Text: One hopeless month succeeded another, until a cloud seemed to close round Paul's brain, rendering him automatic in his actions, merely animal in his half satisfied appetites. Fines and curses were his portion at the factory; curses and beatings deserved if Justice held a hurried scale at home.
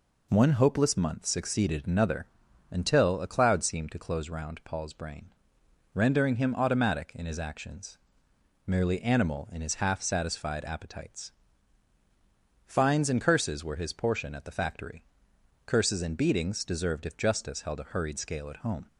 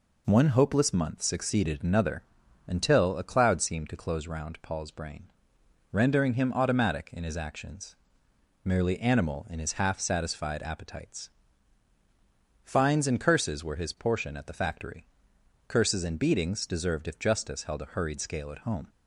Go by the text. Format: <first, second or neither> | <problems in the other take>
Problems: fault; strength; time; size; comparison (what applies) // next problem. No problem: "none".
neither | none